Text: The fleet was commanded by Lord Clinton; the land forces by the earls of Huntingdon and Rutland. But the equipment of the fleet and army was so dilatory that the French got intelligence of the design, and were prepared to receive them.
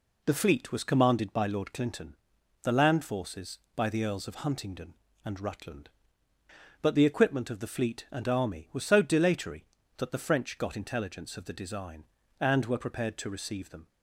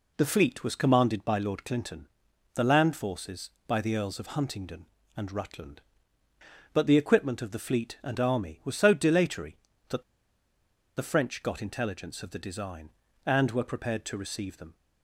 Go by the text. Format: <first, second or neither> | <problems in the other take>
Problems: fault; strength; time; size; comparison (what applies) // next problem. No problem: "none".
first | pauses between "that" and "the"; noticeable; at 10.0 s; 0.93 s long